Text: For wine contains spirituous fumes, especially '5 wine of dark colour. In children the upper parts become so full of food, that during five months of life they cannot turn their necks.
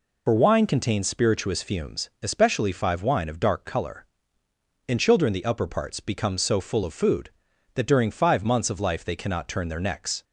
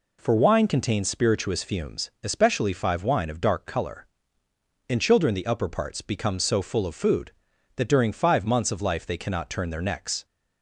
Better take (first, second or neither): second